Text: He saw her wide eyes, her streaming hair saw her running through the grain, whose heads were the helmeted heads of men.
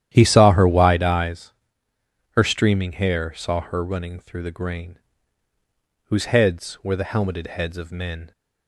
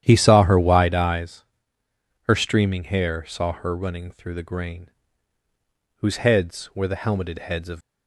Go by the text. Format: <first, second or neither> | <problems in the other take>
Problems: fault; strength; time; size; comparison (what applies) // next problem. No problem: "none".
first | starts louder than the rest; strong; until 1.0 s; 10.5 dB; strong in the first // stops before "men"; at 7.8 s